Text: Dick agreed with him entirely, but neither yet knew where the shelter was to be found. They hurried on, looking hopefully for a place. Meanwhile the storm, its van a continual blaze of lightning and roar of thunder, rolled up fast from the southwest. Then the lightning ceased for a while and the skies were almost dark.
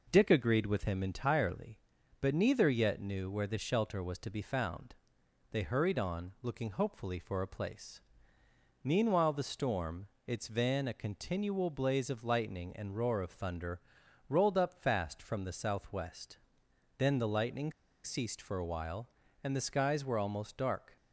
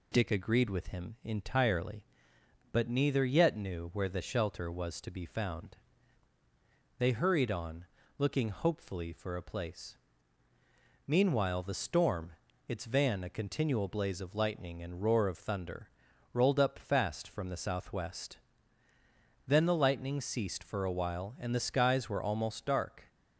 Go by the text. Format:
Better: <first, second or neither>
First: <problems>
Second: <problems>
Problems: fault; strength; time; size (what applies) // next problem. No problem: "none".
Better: second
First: pauses between "lightning" and "ceased"; slight; at 17.7 s; 0.33 s long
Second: none